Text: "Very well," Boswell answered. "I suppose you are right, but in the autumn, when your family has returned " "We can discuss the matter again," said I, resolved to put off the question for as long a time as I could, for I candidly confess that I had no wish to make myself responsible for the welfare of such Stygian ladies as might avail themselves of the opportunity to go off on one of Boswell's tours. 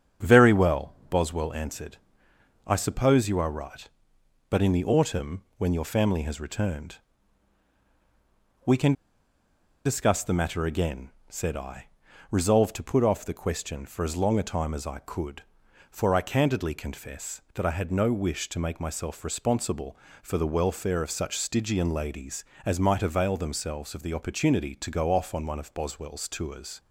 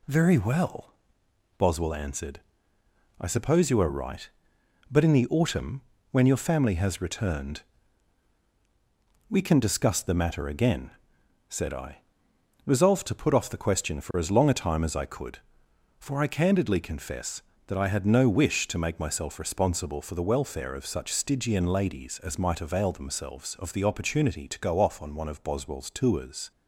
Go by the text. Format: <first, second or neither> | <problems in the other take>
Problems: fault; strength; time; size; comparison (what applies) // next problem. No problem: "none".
second | starts louder than the rest; strong; until 1.3 s; 9.5 dB // pauses between "can" and "discuss"; noticeable; at 8.9 s; 0.92 s long